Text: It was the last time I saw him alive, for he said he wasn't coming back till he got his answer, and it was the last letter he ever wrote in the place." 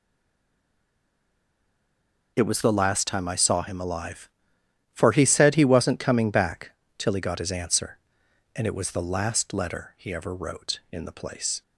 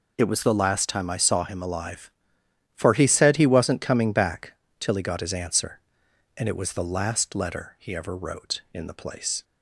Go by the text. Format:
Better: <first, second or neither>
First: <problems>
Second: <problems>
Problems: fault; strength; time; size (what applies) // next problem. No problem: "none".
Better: second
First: stays silent before the first word; until 2.3 s; 2.3 s long // pauses between "back" and "till"; slight; at 6.7 s; 0.24 s long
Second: pauses between "back" and "till"; slight; at 4.5 s; 0.24 s long